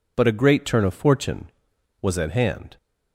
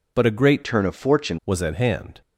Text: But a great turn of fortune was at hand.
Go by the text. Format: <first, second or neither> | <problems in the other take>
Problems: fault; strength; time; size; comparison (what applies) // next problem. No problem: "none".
first | changes voice from "turn" to "fortune"; from 0.6 to 1.3 s; 0.7 s long